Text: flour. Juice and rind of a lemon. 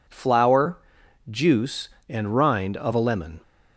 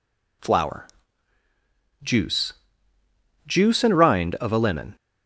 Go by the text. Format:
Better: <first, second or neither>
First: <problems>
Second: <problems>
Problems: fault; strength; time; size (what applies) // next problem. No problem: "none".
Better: first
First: none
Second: says "Juice" twice; at 3.4 s